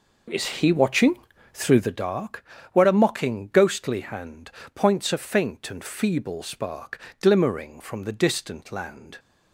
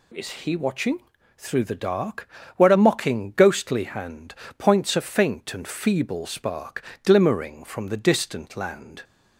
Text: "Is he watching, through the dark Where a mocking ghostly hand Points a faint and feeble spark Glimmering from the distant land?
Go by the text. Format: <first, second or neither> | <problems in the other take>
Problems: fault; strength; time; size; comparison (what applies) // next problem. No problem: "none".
second | starts louder than the rest; noticeable; until 2.1 s; 5 dB // pauses between "dark" and "Where"; slight; at 2.4 s; 0.28 s long; slight in the second // pauses between "hand" and "Points"; slight; at 4.4 s; 0.24 s long; slight in the second // pauses between "spark" and "Glimmering"; slight; at 6.9 s; 0.22 s long; slight in the second